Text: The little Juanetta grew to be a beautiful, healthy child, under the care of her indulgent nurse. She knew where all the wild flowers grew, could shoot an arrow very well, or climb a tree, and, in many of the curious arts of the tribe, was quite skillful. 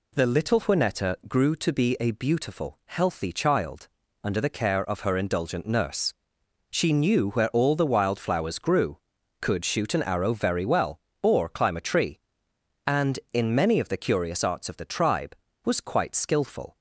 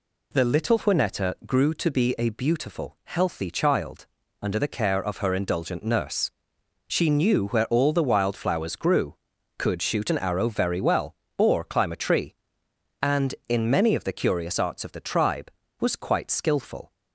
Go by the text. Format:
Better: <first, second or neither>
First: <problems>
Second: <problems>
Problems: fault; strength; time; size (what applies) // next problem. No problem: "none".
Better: neither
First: none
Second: none